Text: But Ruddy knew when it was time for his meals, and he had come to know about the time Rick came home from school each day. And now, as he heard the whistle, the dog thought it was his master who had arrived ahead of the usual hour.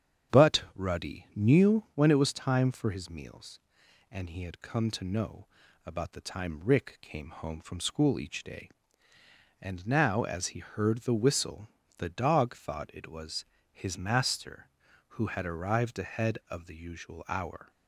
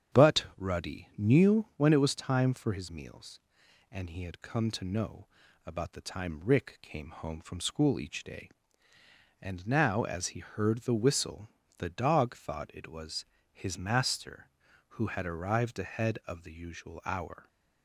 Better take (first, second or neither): neither